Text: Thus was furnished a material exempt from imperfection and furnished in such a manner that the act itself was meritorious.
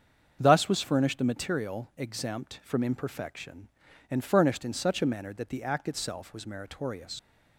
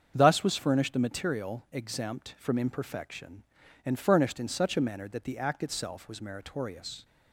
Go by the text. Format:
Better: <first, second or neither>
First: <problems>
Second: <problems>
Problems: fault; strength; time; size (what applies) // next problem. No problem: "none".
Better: second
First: starts louder than the rest; strong; until 1.4 s; 7 dB // leaves "meritorious" unfinished; at 7.1 s; 105 ms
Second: starts louder than the rest; strong; until 1.1 s; 7.5 dB